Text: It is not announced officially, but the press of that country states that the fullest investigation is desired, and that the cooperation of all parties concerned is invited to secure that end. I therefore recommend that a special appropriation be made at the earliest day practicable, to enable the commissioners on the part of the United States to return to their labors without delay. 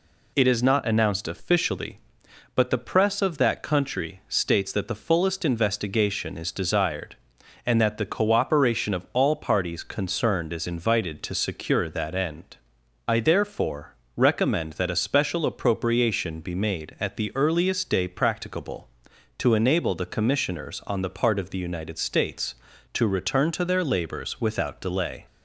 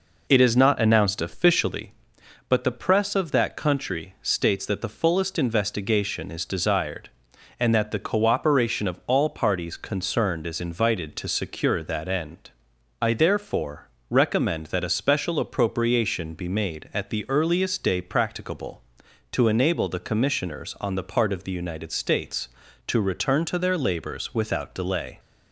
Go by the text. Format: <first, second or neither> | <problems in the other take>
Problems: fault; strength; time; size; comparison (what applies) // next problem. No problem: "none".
first | starts louder than the rest; noticeable; until 1.8 s; 4.5 dB // pauses between "therefore" and "recommend"; slight; at 13.8 s; 0.22 s long; slight in the first